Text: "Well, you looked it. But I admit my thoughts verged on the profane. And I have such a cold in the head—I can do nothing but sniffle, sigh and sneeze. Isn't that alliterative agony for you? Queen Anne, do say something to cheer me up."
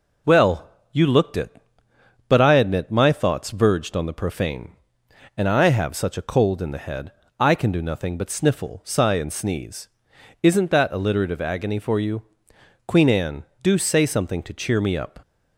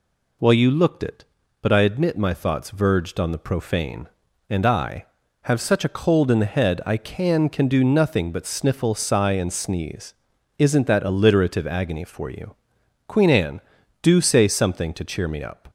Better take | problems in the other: first | says "can" twice; at 7.4 s

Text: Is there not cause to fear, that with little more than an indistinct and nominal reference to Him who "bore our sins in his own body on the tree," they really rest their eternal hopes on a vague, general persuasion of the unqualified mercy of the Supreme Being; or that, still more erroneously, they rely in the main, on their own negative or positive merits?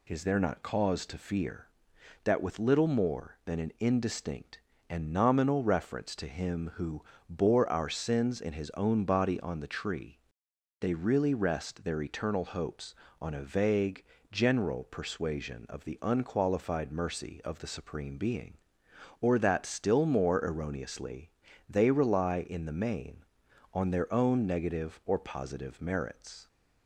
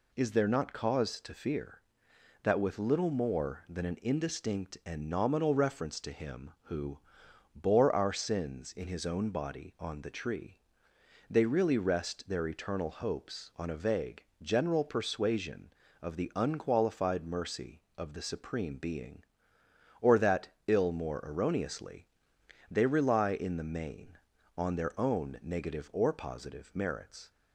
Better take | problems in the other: first | pauses between "who" and "bore"; noticeable; at 6.9 s; 0.56 s long; slight in the first // says "ill" for "still"; at 20.6 s

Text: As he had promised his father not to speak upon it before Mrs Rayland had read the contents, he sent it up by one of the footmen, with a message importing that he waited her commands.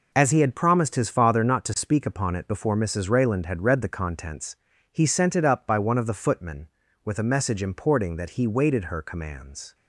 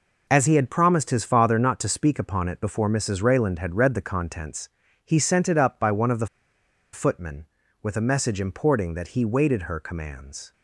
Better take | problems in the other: first | pauses between "the" and "footmen"; noticeable; at 6.2 s; 0.67 s long

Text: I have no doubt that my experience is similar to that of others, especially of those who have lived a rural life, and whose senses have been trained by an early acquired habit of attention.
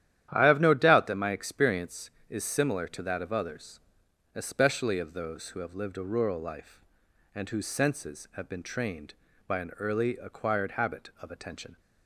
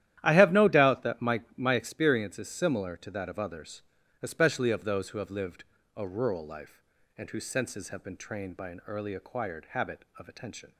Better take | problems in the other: first | starts louder than the rest; strong; until 1.2 s; 12 dB; strong in the first // says "my" twice; at 1.5 s // pauses between "lived" and "a"; slight; at 5.6 s; 0.32 s long

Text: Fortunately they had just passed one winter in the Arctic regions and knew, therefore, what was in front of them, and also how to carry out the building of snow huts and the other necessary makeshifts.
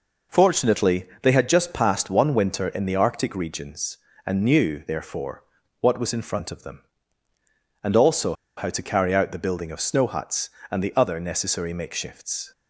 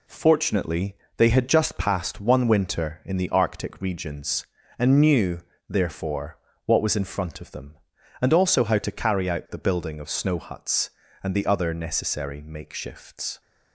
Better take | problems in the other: second | pauses between "Fortunately" and "they"; slight; at 1.0 s; 0.16 s long; slight in the second // pauses between "also" and "how"; slight; at 8.3 s; 0.22 s long

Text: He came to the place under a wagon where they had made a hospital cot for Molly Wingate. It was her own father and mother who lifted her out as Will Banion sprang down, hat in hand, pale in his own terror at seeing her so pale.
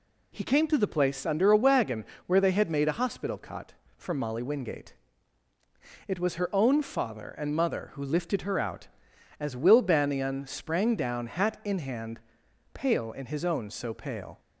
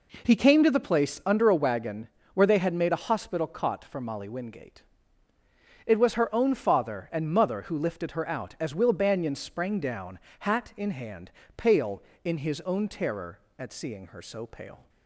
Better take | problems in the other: second | pauses between "wagon" and "where"; slight; at 2.0 s; 0.22 s long; slight in the second // skips "terror at seeing her"; at 13.6 s

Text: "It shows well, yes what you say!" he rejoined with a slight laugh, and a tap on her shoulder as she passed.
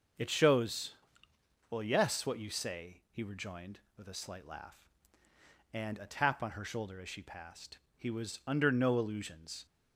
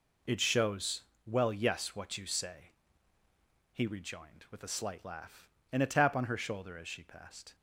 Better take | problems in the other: second | pauses between "shows" and "well"; noticeable; at 0.9 s; 0.76 s long; slight in the second // goes on to say "He was under no illusions"; strong; from 7.9 s on; 1.6 s long

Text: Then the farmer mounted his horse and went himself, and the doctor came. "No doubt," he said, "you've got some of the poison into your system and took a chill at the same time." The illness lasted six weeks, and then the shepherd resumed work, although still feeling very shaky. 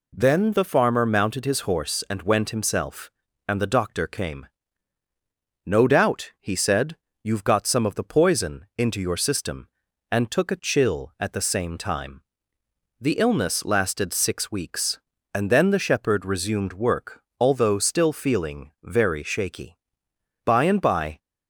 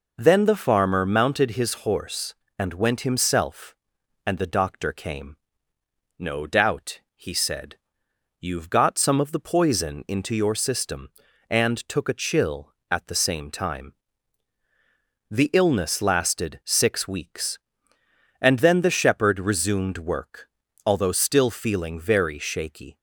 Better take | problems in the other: second | goes on to say "By and by"; noticeable; from 20.4 s on; 0.72 s long

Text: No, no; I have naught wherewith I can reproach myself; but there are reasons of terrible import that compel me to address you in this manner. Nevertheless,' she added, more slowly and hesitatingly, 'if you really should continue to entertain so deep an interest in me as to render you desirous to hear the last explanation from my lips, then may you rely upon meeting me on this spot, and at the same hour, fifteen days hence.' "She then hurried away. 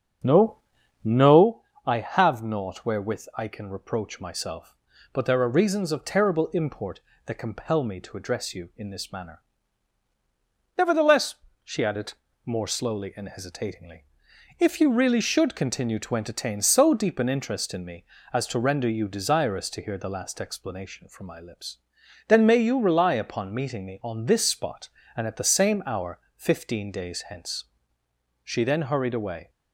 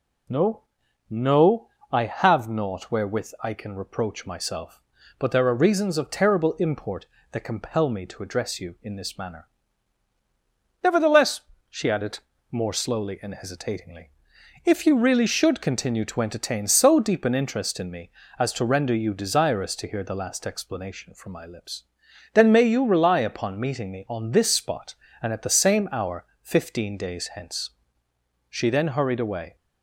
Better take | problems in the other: second | starts louder than the rest; strong; until 1.6 s; 7 dB

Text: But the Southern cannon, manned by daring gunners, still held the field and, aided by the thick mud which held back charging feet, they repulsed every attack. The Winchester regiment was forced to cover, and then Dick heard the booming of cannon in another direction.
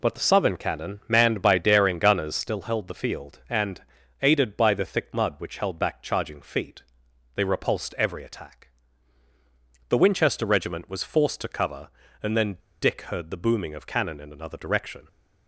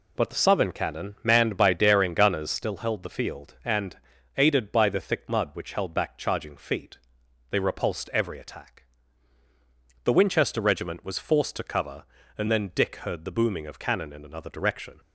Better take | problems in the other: second | pauses between "then" and "Dick"; slight; at 12.5 s; 0.24 s long

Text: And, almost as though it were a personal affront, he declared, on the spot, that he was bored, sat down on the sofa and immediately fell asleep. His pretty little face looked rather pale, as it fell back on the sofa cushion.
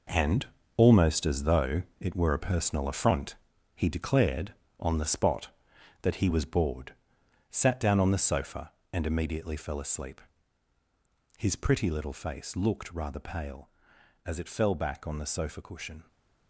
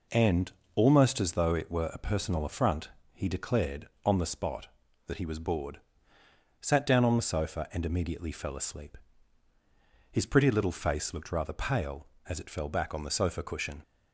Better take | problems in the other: second | gets quieter; strong; throughout; 10 dB // pauses between "though" and "it"; slight; at 1.8 s; 0.18 s long

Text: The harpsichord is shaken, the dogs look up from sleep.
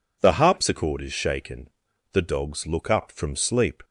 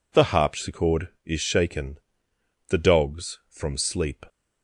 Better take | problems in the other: first | skips "look up"; at 3.4 s

